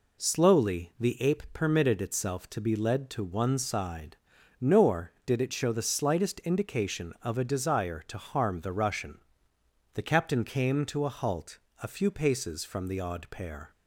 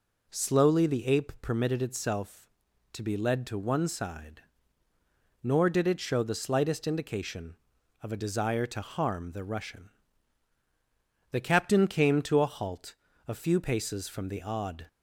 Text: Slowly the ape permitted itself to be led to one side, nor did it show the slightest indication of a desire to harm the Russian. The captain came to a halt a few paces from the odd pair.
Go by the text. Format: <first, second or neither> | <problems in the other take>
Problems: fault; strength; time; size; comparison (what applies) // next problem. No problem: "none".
first | pauses between "halt" and "a"; slight; at 12.9 s; 0.32 s long; slight in the first // stops before "pair"; at 14.8 s